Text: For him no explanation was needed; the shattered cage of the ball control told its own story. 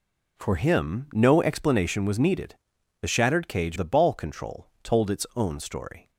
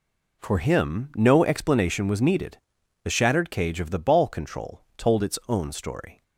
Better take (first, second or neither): second